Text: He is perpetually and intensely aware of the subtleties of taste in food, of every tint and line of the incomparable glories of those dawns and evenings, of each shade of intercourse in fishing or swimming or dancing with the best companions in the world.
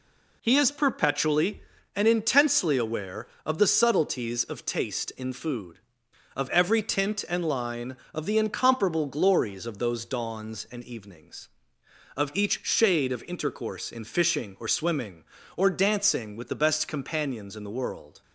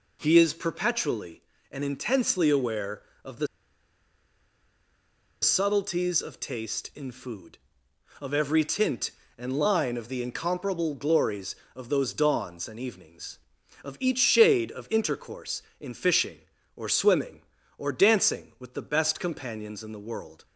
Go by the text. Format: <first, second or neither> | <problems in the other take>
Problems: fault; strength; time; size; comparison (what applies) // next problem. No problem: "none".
first | pauses between "the" and "subtleties"; strong; at 3.4 s; 1.9 s long